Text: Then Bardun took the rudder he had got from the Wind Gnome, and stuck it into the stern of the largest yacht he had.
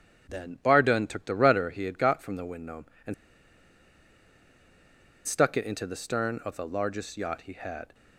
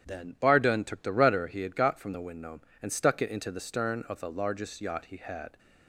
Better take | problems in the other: second | starts louder than the rest; strong; until 1.3 s; 9 dB; strong in the second // pauses between "and" and "stuck"; strong; at 3.1 s; 2.1 s long

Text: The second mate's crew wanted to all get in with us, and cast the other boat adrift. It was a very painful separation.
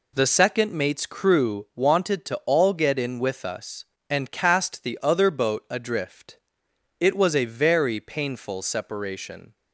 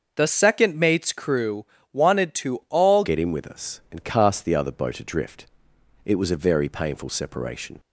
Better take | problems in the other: first | starts louder than the rest; until 1.1 s; 6.5 dB // pauses between "crew" and "wanted"; slight; at 1.6 s; 0.26 s long // changes voice at "get"; from 3.0 s on; 4.7 s long

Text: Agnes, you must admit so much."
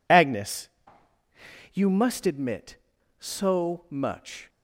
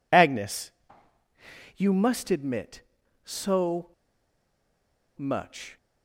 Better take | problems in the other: first | pauses between "so" and "much"; strong; at 3.8 s; 1.2 s long

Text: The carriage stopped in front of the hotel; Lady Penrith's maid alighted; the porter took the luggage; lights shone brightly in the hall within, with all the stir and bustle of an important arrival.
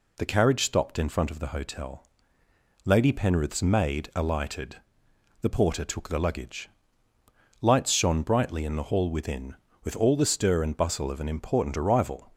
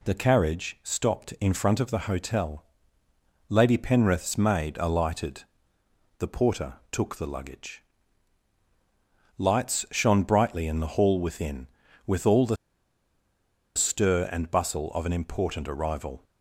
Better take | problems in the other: first | pauses between "porter" and "took"; slight; at 6.7 s; 0.16 s long // pauses between "the" and "stir"; at 12.5 s; 1.1 s long

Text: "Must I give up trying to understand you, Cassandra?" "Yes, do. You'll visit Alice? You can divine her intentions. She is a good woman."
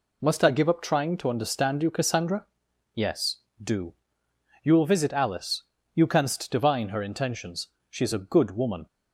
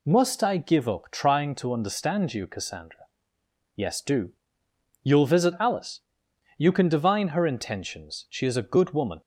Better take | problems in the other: second | says "canst" for "can"; at 6.0 s

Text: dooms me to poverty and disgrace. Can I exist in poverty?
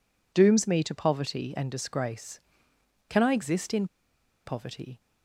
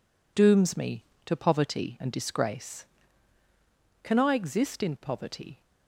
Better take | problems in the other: second | pauses between "in" and "poverty"; noticeable; at 3.8 s; 0.59 s long

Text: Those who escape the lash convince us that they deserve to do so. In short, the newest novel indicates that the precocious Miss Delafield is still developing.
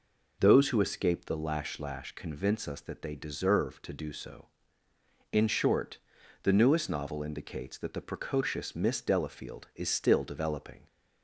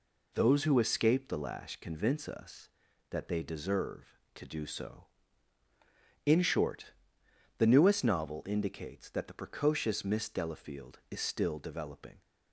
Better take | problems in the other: second | says "lash" twice; at 1.7 s

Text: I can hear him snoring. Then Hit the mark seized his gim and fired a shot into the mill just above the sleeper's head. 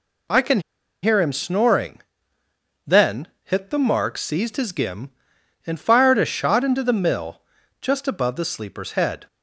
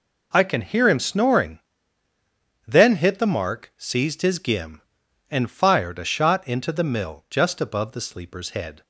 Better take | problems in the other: second | pauses between "can" and "hear"; at 0.5 s; 0.42 s long // pauses between "Then" and "Hit"; slight; at 3.2 s; 0.20 s long // pauses between "mill" and "just"; slight; at 7.4 s; 0.36 s long

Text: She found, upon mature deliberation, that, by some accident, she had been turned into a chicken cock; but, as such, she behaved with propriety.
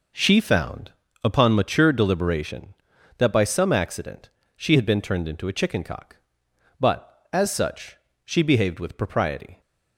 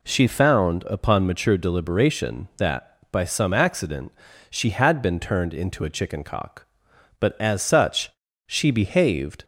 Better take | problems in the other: first | stops before "with propriety"; at 9.4 s

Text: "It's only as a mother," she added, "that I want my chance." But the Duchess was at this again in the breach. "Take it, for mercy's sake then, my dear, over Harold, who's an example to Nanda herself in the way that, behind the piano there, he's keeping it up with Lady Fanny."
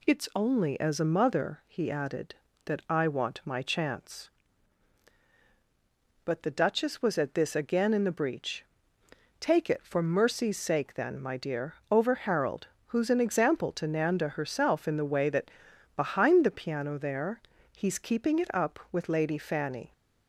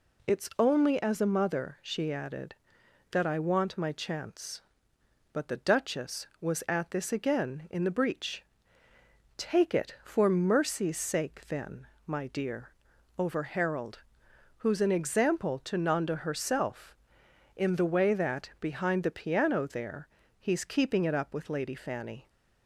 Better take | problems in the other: second | says "he" for "she"; at 1.6 s

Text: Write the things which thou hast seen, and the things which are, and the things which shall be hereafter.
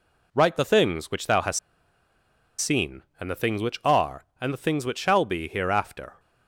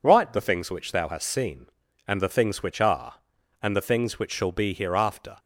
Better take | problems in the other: second | pauses between "hast" and "seen"; at 1.5 s; 1.0 s long

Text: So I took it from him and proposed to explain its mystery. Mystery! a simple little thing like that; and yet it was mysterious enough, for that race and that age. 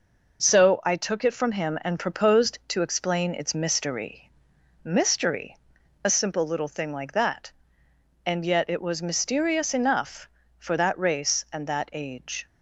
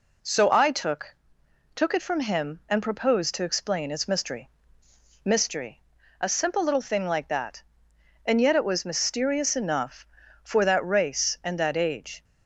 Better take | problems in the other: first | says "took" twice; at 1.7 s

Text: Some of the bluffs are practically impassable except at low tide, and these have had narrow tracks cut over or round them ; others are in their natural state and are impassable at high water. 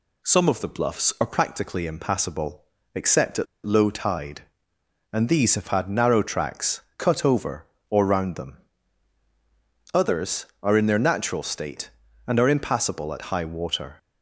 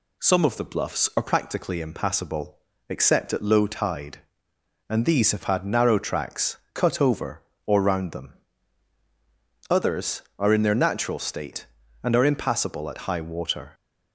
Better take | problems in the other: second | pauses between "impassable" and "except"; slight; at 2.6 s; 0.32 s long; slight in the second // pauses between "at" and "low"; slight; at 3.4 s; 0.19 s long // pauses between "tracks" and "cut"; slight; at 6.7 s; 0.16 s long; slight in the second

